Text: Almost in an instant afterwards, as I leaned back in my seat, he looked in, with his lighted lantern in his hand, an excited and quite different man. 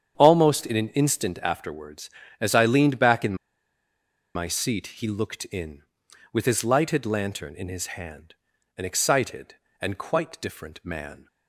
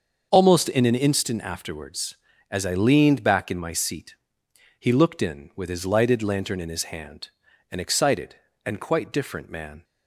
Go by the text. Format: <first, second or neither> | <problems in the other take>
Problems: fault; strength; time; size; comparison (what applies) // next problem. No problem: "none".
second | starts louder than the rest; strong; until 1.1 s; 8 dB; also in the second // pauses between "in" and "my"; at 3.3 s; 1.0 s long